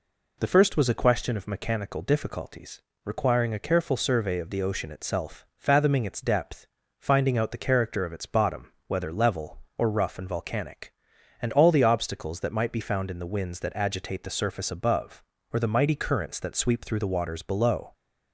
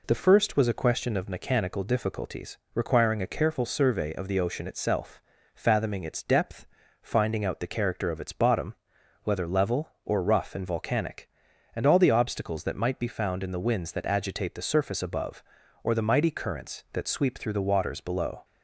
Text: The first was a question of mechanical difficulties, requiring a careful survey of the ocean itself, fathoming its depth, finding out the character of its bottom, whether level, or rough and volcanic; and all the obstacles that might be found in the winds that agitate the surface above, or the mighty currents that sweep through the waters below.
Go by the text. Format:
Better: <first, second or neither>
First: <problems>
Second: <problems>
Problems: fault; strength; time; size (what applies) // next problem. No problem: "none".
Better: neither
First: none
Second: none